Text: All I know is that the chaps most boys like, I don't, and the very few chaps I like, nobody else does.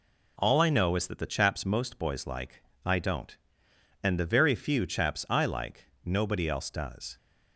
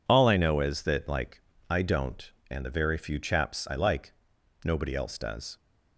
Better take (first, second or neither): first